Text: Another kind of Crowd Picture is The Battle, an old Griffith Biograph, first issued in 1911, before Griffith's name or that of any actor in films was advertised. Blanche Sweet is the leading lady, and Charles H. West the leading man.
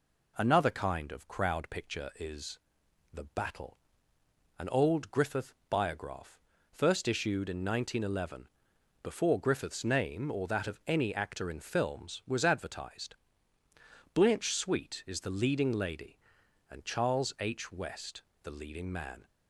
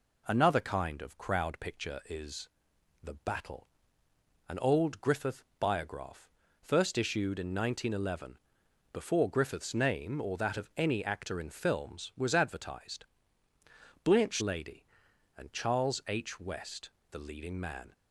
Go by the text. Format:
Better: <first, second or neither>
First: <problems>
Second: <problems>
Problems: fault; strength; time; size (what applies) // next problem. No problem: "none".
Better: first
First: pauses between "is" and "The"; noticeable; at 2.5 s; 0.54 s long // pauses between "West" and "the"; slight; at 18.2 s; 0.22 s long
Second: pauses between "is" and "The"; noticeable; at 2.4 s; 0.54 s long // skips "Sweet is the leading"; at 14.4 s // pauses between "West" and "the"; slight; at 16.9 s; 0.22 s long